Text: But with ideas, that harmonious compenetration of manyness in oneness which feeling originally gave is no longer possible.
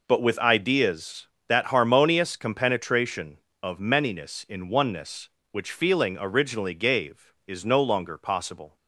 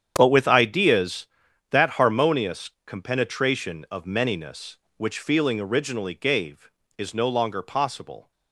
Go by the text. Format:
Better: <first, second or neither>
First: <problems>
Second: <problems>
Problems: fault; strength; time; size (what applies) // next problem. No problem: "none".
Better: first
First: none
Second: starts louder than the rest; strong; until 1.1 s; 8.5 dB // pauses between "harmonious" and "compenetration"; slight; at 2.7 s; 0.16 s long // skips "in oneness"; at 4.8 s